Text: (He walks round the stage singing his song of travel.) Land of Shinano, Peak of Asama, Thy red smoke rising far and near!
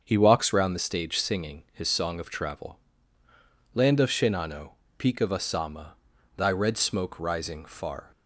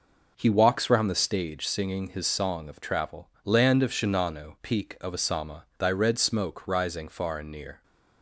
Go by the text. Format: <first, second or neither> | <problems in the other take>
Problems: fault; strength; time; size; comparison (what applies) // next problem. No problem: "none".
second | starts louder than the rest; until 1.0 s; 6.5 dB // stops before "and near"; at 8.1 s